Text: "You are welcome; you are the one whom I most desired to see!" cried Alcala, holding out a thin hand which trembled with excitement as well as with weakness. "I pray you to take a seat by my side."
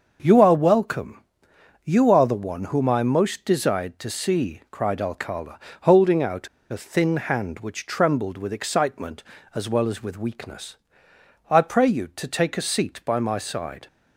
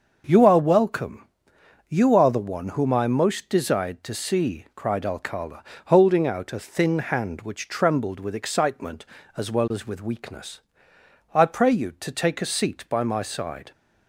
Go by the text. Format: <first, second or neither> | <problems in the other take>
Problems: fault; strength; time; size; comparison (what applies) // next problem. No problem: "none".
second | starts louder than the rest; until 1.2 s; 6.5 dB; also in the second // pauses between "out" and "a"; slight; at 6.4 s; 0.23 s long